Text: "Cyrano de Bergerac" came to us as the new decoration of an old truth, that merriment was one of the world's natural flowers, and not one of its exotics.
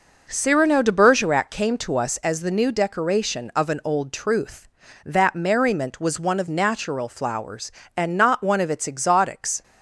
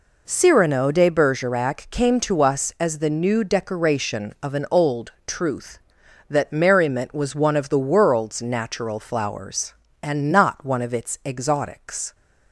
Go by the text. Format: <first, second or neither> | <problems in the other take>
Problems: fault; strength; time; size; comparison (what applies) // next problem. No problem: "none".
second | skips "the world's"; at 6.4 s